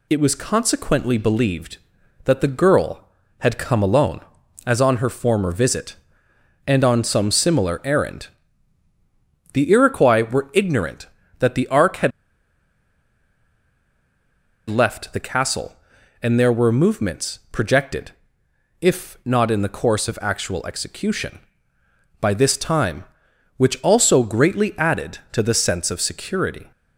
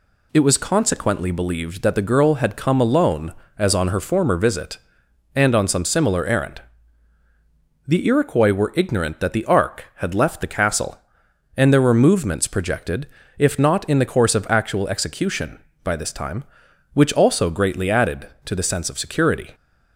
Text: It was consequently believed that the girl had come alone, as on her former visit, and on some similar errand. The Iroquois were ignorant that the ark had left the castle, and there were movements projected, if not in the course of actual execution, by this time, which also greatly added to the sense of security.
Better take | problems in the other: second | pauses between "had" and "left"; strong; at 12.1 s; 2.5 s long

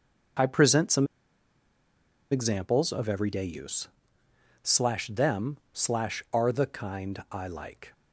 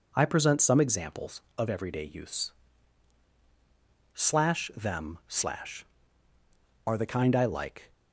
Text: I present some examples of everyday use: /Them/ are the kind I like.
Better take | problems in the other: second | pauses between "some" and "examples"; strong; at 1.0 s; 1.2 s long

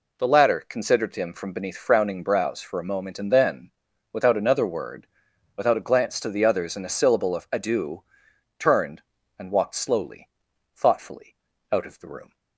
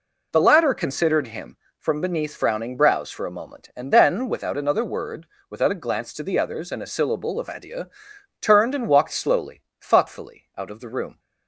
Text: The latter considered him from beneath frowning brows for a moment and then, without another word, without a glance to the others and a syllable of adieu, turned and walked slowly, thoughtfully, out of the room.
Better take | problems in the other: neither | none

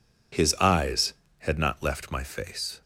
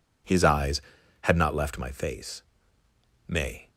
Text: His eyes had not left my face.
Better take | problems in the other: first | goes on to say "May"; slight; from 3.2 s on; 0.42 s long

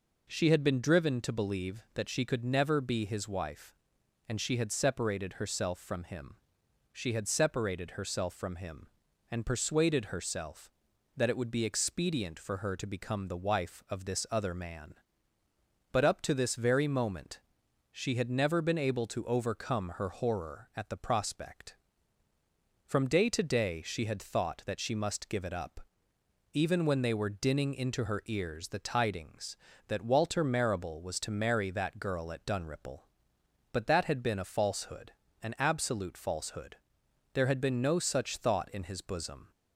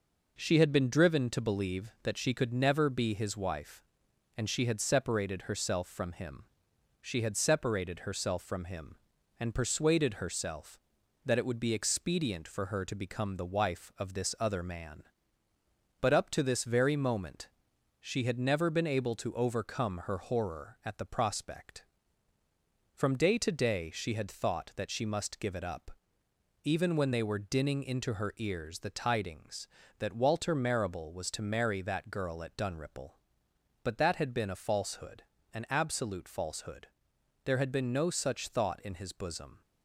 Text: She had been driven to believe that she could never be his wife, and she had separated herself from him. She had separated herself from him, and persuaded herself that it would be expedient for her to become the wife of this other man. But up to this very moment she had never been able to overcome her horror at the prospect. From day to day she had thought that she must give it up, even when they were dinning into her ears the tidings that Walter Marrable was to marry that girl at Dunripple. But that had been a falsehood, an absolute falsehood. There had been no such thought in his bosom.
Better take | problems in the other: first | gets quieter; noticeable; throughout; 4 dB // pauses between "moment" and "she"; noticeable; at 17.4 s; 0.50 s long; noticeable in the first

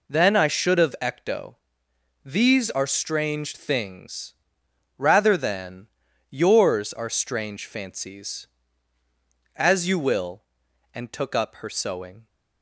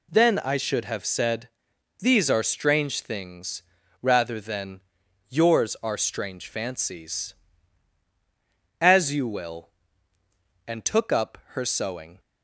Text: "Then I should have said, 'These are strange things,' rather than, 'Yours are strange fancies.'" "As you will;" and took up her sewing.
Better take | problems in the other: second | says "ecto" for "said"; at 1.0 s

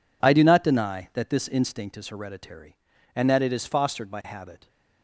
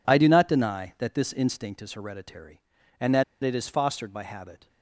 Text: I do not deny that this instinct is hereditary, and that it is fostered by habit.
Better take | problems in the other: first | pauses between "that" and "it"; slight; at 3.2 s; 0.19 s long

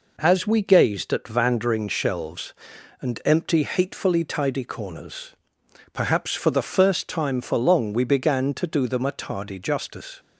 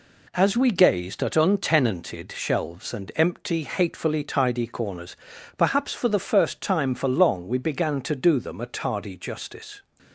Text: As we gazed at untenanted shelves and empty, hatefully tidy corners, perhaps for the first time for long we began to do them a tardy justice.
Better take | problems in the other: second | says "vandering" for "untenanted"; at 1.2 s

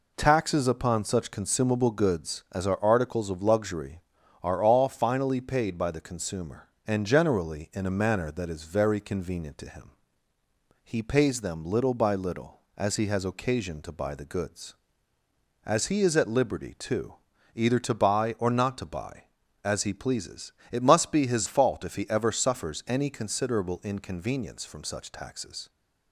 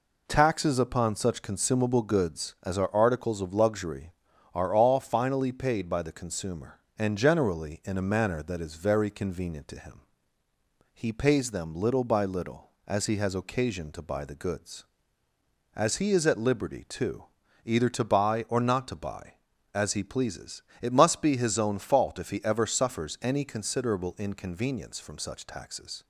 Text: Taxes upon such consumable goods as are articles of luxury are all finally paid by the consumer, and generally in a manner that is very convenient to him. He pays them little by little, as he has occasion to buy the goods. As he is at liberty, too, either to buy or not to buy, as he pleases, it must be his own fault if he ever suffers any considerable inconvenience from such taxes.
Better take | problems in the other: second | skips "own"; at 21.4 s

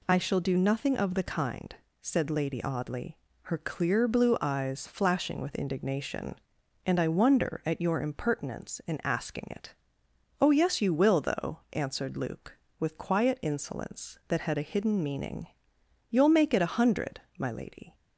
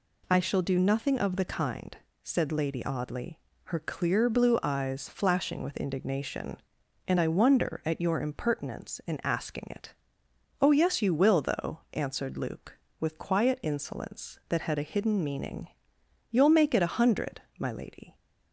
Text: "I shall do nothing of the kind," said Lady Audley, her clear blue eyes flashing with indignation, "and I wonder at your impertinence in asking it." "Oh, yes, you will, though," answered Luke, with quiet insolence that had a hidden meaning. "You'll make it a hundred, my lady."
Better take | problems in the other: neither | none

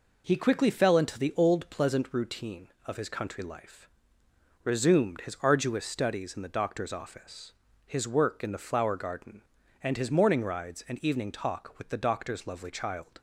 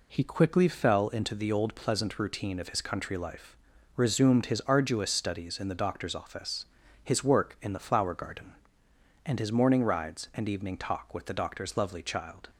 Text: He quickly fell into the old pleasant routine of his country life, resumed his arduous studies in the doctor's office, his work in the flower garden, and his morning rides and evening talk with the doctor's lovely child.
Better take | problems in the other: neither | none

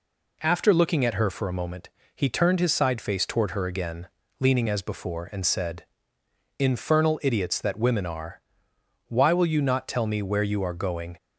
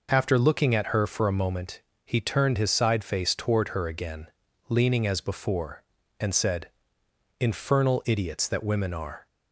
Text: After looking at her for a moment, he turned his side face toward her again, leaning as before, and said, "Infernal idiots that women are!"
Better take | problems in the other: second | goes on to say "Why will you not tell me where you are going"; strong; from 9.0 s on; 2.0 s long

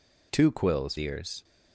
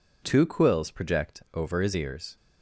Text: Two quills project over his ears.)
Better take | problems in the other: second | skips "project over his"; at 0.9 s

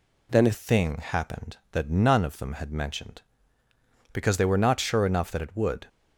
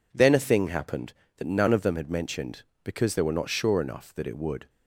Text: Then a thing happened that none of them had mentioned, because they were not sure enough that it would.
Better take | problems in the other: second | changes voice at "thing"; from 0.5 s on; 5.3 s long

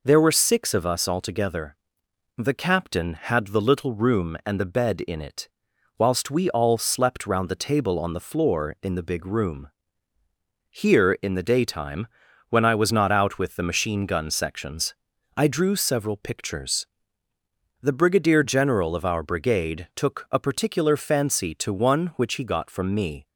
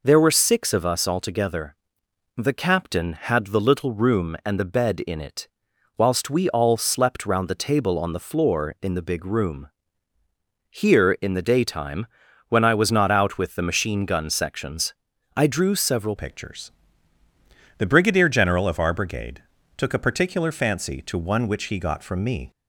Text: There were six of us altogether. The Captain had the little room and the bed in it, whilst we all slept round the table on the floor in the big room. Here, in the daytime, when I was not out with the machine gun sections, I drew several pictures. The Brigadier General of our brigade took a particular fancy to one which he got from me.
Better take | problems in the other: first | changes voice at "pictures"; from 16.1 s on; 6.4 s long // pauses between "brigade" and "took"; slight; at 19.4 s; 0.34 s long

